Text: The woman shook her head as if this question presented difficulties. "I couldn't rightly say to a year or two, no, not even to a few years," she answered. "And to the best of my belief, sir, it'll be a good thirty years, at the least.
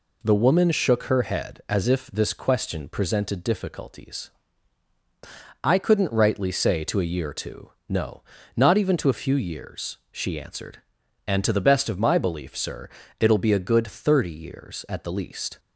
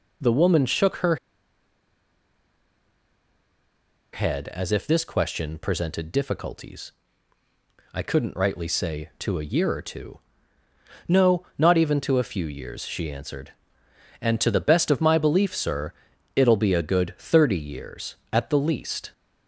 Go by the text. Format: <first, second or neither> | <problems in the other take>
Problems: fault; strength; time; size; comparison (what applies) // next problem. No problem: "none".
first | pauses between "her" and "head"; strong; at 1.1 s; 2.9 s long